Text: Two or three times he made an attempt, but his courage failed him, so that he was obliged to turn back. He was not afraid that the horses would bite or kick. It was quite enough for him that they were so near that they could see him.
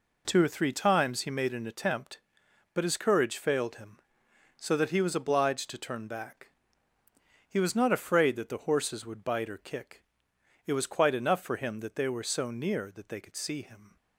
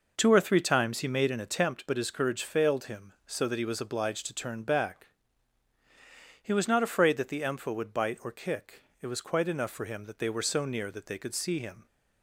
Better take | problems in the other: first | says "empha" for "horses"; at 7.4 s

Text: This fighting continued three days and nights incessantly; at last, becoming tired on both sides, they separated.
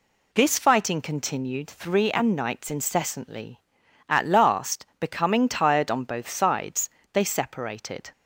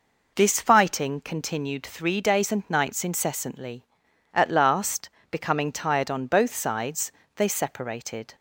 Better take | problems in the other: second | skips "days"; at 2.0 s

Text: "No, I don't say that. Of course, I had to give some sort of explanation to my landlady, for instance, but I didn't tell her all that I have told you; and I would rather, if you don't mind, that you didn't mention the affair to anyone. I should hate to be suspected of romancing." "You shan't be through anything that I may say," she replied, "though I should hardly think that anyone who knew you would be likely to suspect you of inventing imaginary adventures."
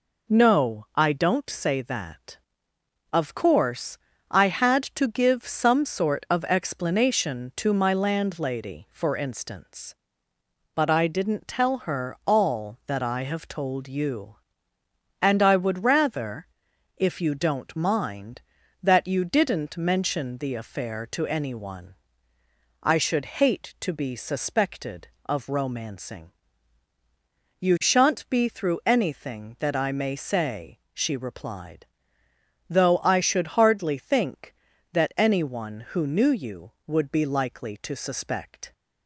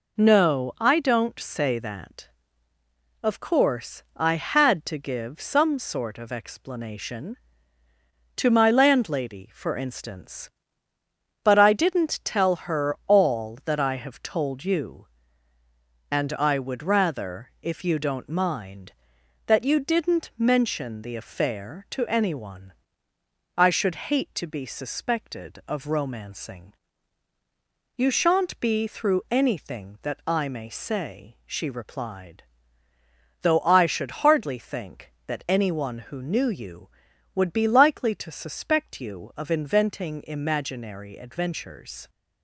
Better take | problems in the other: second | stops before "you of inventing imaginary adventures"; at 38.7 s

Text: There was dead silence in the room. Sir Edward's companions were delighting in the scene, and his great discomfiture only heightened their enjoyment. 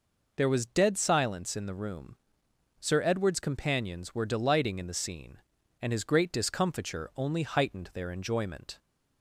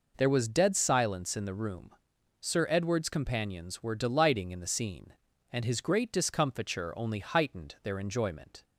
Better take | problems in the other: neither | none

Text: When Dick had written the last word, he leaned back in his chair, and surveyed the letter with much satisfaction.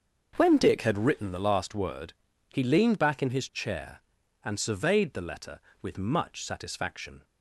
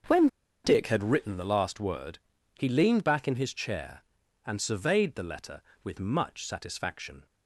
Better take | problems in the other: first | starts louder than the rest; until 1.4 s; 6.5 dB; also in the first // pauses between "When" and "Dick"; at 0.2 s; 0.37 s long

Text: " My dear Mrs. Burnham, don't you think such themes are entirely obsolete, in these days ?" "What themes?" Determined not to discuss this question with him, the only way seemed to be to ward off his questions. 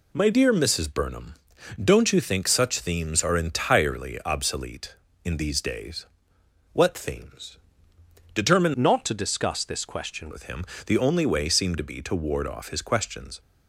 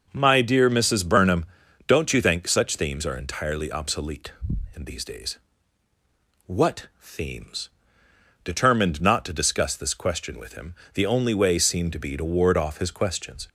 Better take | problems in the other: second | changes voice from "not" to "question"; from 8.7 to 10.3 s; 1.6 s long

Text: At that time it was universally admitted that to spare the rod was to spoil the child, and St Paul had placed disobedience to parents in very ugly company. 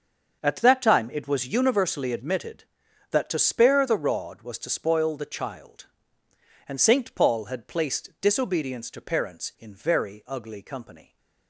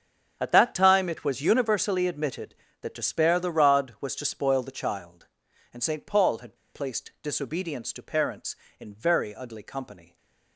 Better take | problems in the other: first | starts louder than the rest; strong; until 1.4 s; 7.5 dB; also in the first // pauses between "had" and "placed"; slight; at 6.5 s; 0.18 s long

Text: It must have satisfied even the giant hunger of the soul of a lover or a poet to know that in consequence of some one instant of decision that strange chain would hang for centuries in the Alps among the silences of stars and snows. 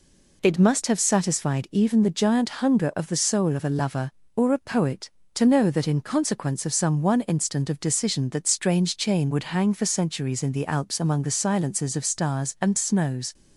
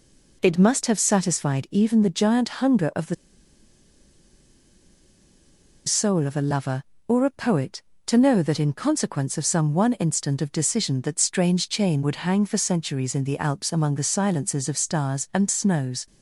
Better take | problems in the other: first | pauses between "the" and "soul"; strong; at 3.1 s; 2.7 s long

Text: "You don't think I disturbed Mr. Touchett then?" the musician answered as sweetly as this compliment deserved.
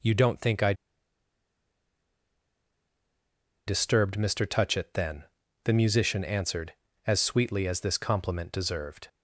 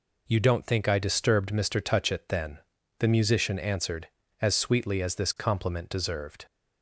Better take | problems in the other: second | pauses between "I" and "disturbed"; strong; at 0.7 s; 2.9 s long

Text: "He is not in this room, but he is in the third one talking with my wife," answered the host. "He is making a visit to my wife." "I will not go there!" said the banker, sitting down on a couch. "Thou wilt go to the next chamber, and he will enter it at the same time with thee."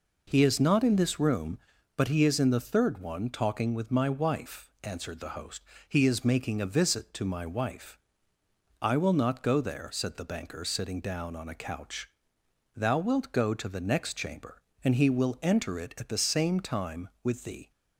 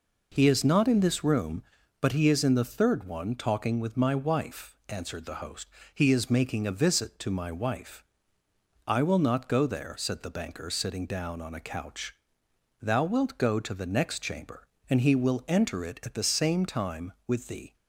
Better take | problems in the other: neither | none

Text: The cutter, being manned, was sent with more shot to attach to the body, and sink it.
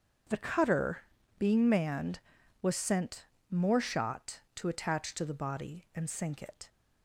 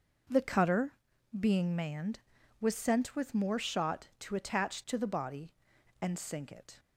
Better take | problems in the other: second | starts louder than the rest; until 1.6 s; 7 dB // skips "with"; at 3.3 s

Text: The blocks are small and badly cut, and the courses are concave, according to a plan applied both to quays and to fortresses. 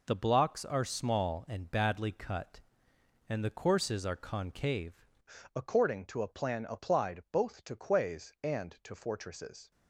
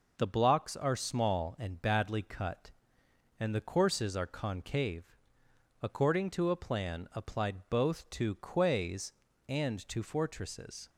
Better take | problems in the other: second | changes voice at "according"; from 5.5 s on; 4.2 s long

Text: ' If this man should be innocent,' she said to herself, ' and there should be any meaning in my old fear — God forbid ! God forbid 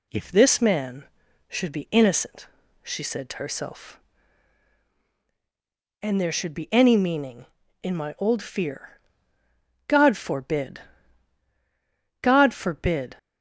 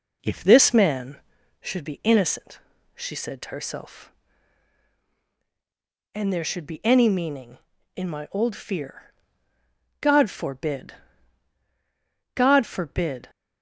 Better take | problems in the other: first | starts louder than the rest; noticeable; until 1.5 s; 5 dB

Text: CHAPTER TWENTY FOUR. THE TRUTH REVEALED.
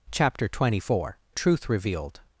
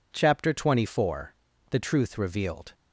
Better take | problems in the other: second | skips "THE"; at 1.2 s

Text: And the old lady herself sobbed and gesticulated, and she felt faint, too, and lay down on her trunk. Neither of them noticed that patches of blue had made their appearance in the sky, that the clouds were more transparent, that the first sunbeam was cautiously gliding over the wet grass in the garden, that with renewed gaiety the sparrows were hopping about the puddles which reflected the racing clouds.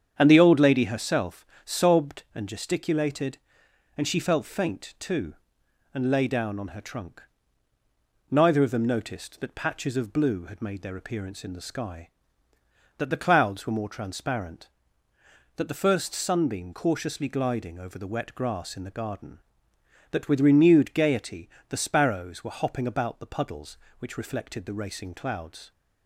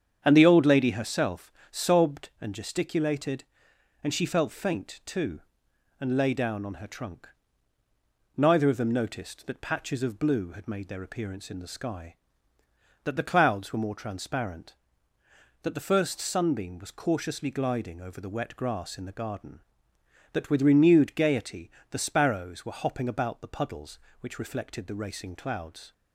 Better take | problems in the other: second | starts louder than the rest; strong; until 1.1 s; 8 dB; strong in the second // pauses between "herself" and "sobbed"; slight; at 1.4 s; 0.20 s long; slight in the second // skips "was"; at 16.7 s // pauses between "gaiety" and "the"; slight; at 21.4 s; 0.22 s long; slight in the second

